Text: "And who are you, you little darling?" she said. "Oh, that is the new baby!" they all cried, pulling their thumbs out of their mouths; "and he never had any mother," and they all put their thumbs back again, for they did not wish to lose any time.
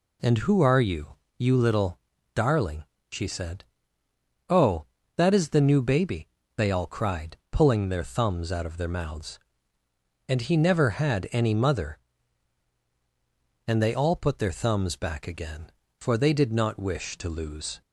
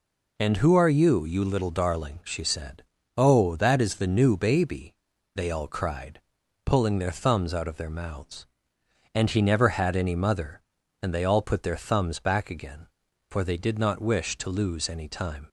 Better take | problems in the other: second | pauses between "little" and "darling"; at 1.9 s; 0.38 s long // stops before "any time"; at 17.8 s

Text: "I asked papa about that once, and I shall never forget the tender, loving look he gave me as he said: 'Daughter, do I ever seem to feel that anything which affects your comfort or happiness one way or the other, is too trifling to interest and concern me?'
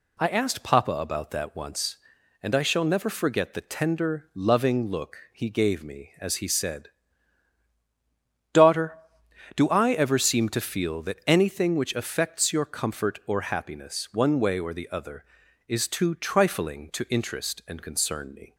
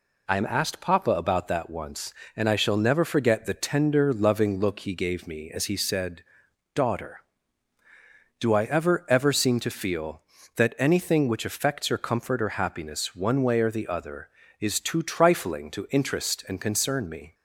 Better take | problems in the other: first | says "ever" twice; at 9.0 s

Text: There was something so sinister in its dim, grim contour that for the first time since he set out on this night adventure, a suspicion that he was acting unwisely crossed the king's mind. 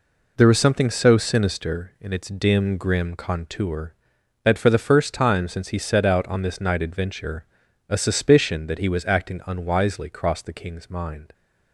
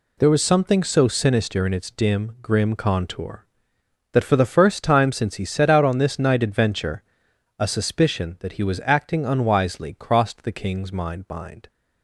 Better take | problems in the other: first | says "mind" twice; at 11.2 s

